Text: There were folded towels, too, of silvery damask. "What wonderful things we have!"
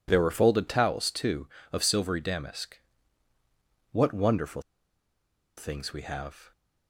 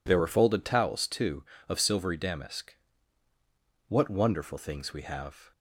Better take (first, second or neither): second